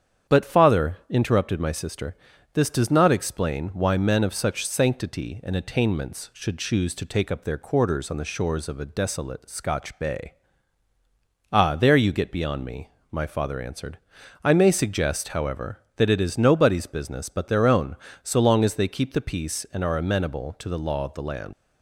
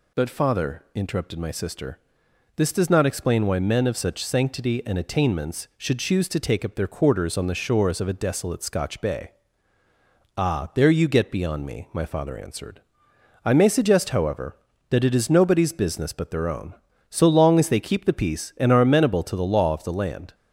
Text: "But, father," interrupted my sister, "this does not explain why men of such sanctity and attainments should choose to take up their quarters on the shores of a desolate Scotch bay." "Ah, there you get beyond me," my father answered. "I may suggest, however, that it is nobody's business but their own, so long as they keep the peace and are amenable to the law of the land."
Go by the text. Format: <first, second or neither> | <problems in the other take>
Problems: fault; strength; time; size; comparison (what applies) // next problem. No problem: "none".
second | starts louder than the rest; strong; until 1.4 s; 8.5 dB // leaves "land" unfinished; at 21.5 s; 85 ms